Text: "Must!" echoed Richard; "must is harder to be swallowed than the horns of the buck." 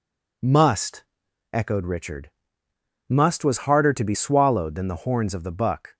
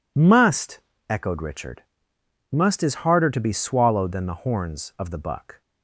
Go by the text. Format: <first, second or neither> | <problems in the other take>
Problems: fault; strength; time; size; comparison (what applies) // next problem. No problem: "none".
second | says "was" for "is"; at 3.4 s